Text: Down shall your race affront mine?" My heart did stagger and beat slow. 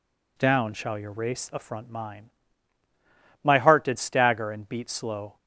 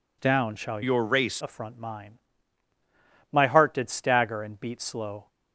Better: first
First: none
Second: changes voice from "your" to "race"; from 0.8 to 1.4 s; 0.6 s long

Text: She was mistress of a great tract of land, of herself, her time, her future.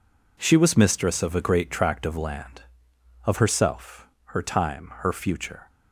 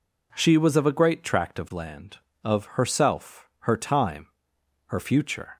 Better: first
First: none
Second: skips "mistress"; at 0.7 s

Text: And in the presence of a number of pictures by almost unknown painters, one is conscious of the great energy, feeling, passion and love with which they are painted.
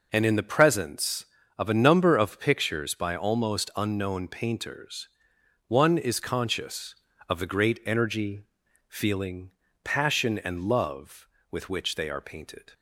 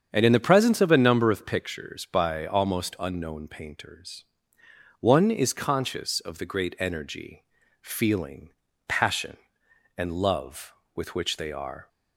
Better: first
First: none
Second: starts louder than the rest; strong; until 1.1 s; 7.5 dB // stops before "painted"; at 11.8 s

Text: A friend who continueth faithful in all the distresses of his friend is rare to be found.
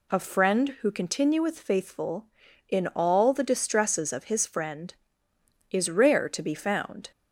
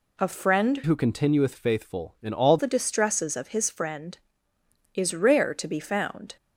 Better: first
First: none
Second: changes voice from "who" to "all"; from 0.8 to 2.5 s; 1.7 s long

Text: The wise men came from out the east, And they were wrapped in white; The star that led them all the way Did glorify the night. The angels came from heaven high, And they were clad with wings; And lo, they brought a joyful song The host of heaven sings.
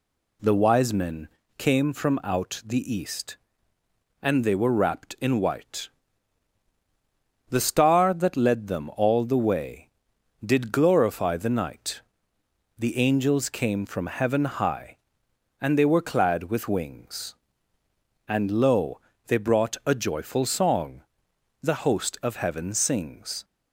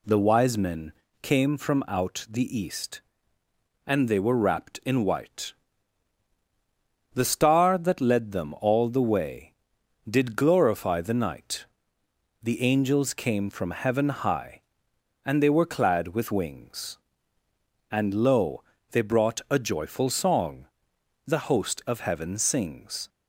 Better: neither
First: pauses between "men" and "came"; slight; at 1.2 s; 0.30 s long // pauses between "song" and "The"; noticeable; at 21.0 s; 0.62 s long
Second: pauses between "men" and "came"; slight; at 0.9 s; 0.30 s long // pauses between "song" and "The"; noticeable; at 20.6 s; 0.62 s long

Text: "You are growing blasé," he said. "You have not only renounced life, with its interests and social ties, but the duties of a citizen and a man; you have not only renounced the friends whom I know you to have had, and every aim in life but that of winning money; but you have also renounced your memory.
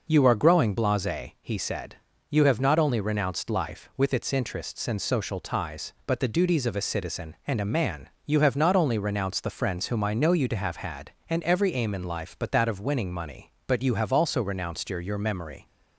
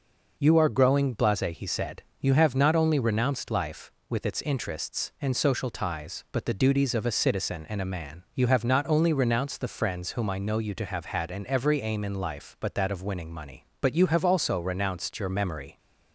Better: second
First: says "your" twice; at 15.0 s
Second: none

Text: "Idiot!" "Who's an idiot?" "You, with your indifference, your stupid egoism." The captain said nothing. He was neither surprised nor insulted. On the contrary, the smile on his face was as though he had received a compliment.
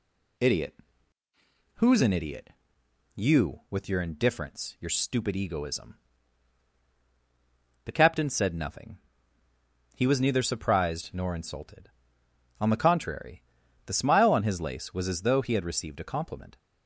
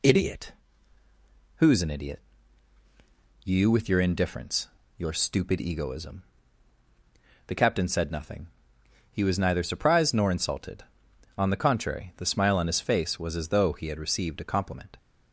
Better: second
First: says "lace" for "face"; at 14.6 s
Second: none

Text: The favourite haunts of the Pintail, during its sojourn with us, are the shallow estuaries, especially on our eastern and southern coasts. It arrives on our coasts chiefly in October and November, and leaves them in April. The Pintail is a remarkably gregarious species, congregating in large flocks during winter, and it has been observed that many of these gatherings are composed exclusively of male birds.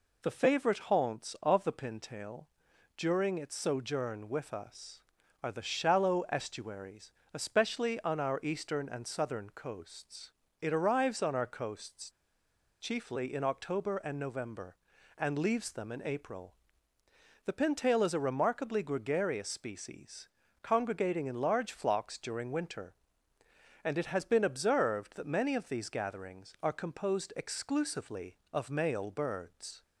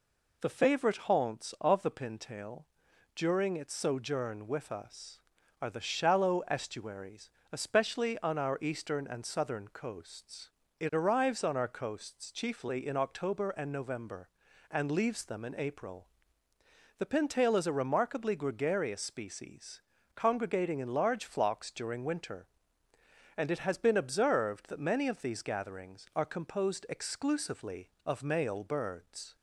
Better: second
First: pauses between "coasts" and "chiefly"; noticeable; at 12.0 s; 0.70 s long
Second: none

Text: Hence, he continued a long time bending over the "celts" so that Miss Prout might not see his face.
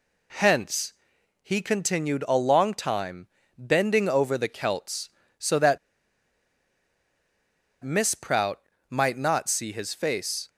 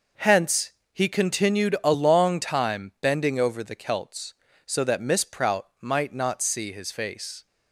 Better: second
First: pauses between "time" and "bending"; slight; at 3.2 s; 0.30 s long // pauses between "that" and "Miss"; strong; at 5.7 s; 2.0 s long // pauses between "Prout" and "might"; slight; at 8.6 s; 0.30 s long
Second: none

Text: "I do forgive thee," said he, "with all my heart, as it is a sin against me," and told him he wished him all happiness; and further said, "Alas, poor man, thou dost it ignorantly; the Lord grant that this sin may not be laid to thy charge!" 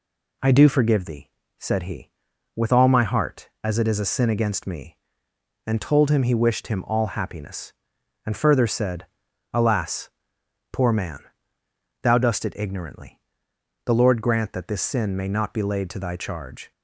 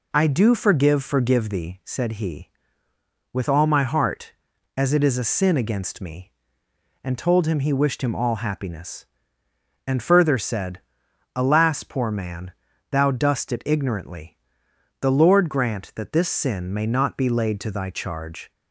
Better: first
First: none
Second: says "forgive" twice; at 1.0 s

